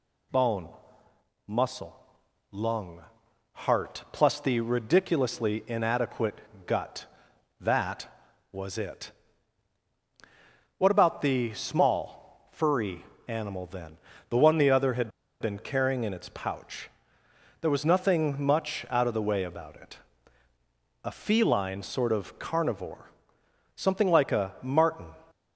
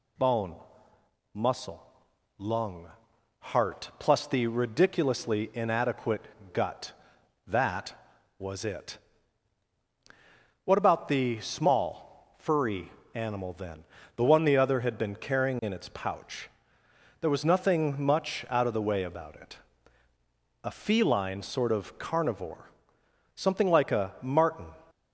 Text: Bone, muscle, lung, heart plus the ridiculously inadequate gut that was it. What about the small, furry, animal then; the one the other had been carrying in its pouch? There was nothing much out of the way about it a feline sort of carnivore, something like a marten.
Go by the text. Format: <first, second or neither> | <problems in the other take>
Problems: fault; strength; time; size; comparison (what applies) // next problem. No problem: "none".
second | pauses between "inadequate" and "gut"; slight; at 6.4 s; 0.24 s long; slight in the second // pauses between "had" and "been"; slight; at 15.0 s; 0.31 s long // pauses between "it" and "a"; at 19.9 s; 1.0 s long; also in the second